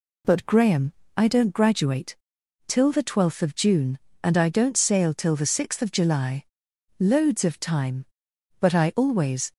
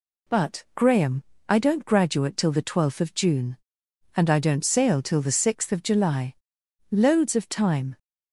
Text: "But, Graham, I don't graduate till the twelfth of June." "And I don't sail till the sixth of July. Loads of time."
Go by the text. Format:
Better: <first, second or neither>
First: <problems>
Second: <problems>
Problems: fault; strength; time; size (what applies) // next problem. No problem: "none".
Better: second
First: pauses between "graduate" and "till"; noticeable; at 2.1 s; 0.50 s long // goes on to say "But I always"; noticeable; from 8.5 s on; 0.92 s long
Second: none